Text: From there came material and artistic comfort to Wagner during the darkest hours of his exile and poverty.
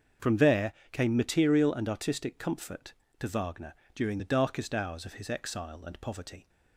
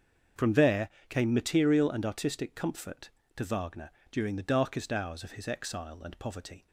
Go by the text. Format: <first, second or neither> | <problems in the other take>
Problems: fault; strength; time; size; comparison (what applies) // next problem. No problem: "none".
neither | starts louder than the rest; the same in both // pauses between "there" and "came"; slight; the same in both // pauses between "Wagner" and "during"; slight; the same in both